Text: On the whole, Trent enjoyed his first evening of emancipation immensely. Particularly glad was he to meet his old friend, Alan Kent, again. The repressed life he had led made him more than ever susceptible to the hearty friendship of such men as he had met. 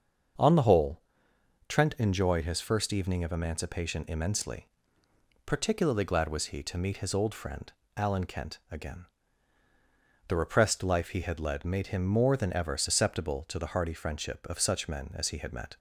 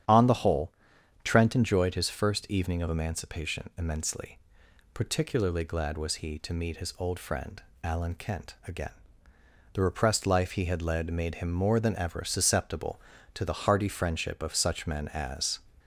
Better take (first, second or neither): first